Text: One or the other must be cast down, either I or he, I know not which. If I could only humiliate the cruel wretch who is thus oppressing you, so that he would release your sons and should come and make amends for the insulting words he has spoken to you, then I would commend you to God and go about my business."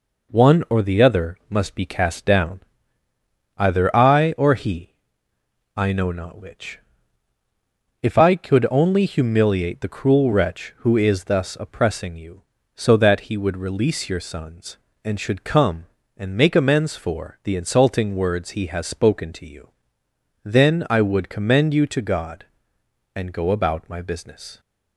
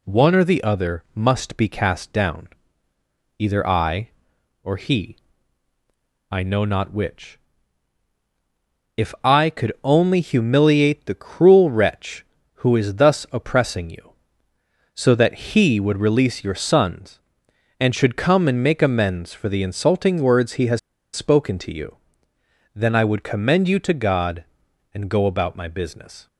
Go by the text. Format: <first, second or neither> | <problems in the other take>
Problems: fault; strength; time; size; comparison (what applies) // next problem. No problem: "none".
first | pauses between "has" and "spoken"; slight; at 20.7 s; 0.35 s long